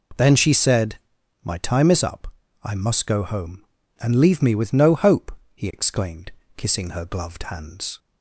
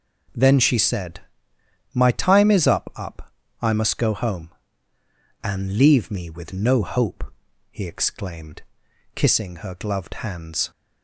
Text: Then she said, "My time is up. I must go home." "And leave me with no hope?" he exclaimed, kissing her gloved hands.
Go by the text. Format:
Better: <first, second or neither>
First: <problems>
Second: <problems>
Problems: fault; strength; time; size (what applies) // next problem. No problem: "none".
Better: first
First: none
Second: says "up" twice; at 2.9 s